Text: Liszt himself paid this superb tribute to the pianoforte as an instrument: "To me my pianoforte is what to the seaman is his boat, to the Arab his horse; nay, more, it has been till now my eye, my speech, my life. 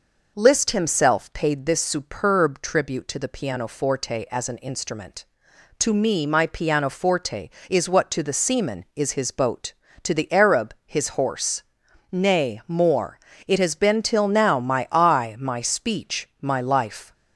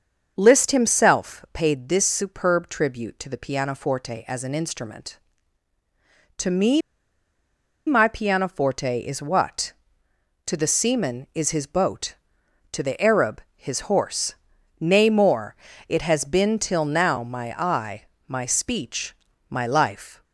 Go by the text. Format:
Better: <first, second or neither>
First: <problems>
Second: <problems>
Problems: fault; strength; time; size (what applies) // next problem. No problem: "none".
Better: first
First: none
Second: starts louder than the rest; until 1.3 s; 6.5 dB // pauses between "me" and "my"; at 6.8 s; 1.0 s long